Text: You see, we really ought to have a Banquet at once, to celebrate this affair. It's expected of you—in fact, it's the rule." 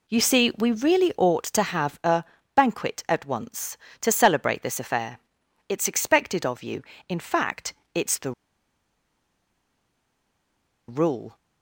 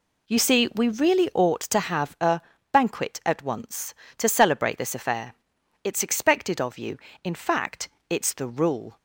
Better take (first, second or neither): second